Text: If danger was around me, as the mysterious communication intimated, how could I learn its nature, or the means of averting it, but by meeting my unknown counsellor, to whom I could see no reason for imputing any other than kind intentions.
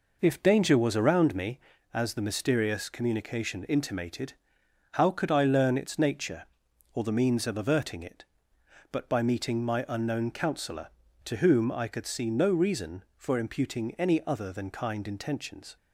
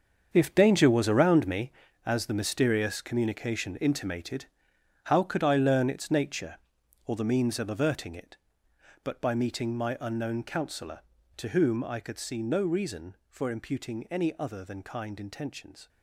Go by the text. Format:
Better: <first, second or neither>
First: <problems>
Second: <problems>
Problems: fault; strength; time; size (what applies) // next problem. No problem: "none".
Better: first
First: none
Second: gets quieter; strong; throughout; 11.5 dB